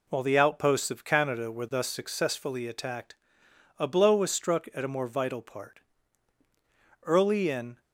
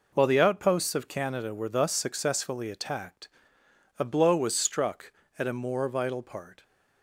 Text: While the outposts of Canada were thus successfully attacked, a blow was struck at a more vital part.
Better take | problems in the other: second | goes on to say "Early in"; noticeable; from 7.0 s on; 0.76 s long

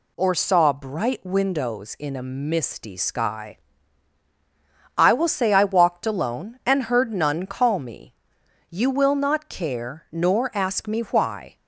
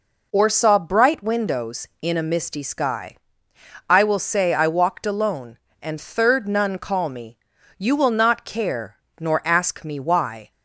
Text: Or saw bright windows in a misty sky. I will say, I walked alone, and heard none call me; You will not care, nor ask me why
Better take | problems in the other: first | says "third" for "heard"; at 6.0 s

